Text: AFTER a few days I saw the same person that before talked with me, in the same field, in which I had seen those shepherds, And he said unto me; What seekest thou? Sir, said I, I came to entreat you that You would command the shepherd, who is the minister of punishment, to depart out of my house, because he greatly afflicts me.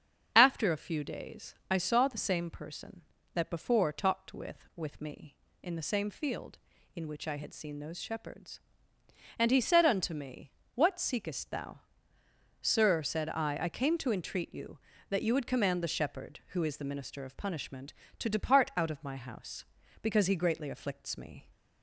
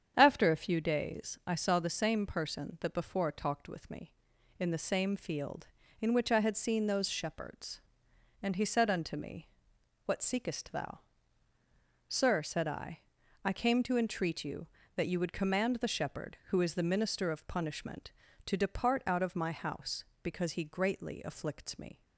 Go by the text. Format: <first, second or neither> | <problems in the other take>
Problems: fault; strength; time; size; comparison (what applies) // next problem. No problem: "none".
second | starts louder than the rest; strong; until 1.3 s; 7.5 dB; strong in the second // says "with" twice; at 4.7 s